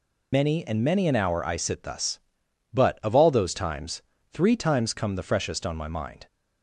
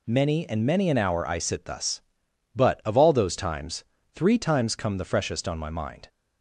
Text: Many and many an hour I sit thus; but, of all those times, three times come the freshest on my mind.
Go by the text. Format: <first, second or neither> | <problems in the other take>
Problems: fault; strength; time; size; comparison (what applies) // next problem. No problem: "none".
second | loses the start of "Many"; at 0.3 s; 85 ms